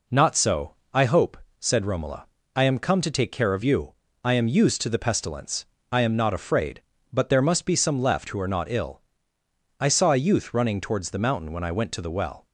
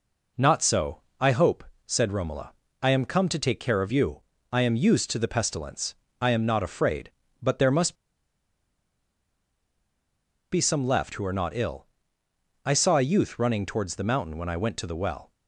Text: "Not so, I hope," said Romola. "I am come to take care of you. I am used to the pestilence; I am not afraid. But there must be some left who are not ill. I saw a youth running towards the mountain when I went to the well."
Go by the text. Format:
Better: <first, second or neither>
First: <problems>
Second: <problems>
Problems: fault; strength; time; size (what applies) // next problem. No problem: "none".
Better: first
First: none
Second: pauses between "must" and "be"; strong; at 7.9 s; 2.5 s long